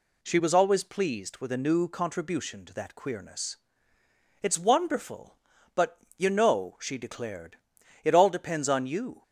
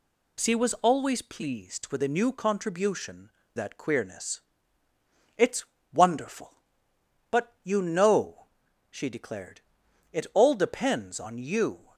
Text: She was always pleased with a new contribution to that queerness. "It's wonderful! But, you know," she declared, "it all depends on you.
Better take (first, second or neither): first